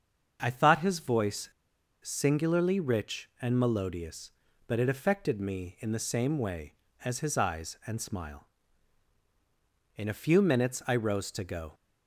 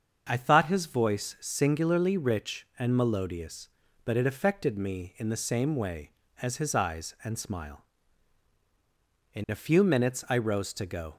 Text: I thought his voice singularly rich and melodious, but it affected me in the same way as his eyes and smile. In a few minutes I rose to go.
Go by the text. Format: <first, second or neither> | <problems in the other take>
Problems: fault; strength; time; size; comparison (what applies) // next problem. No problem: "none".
second | starts louder than the rest; until 1.4 s; 7 dB; also in the second // pauses between "voice" and "singularly"; noticeable; at 1.4 s; 0.53 s long